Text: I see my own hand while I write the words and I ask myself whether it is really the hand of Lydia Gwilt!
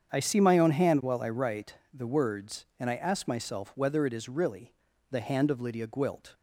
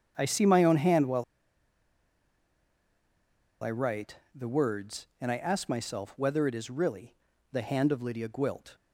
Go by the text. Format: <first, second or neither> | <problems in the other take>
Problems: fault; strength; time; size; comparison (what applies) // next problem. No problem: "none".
first | starts louder than the rest; strong; until 1.1 s; 8 dB; strong in the first // pauses between "while" and "I"; strong; at 1.2 s; 2.3 s long // pauses between "write" and "the"; slight; at 4.1 s; 0.18 s long; slight in the first // pauses between "really" and "the"; slight; at 7.1 s; 0.36 s long; slight in the first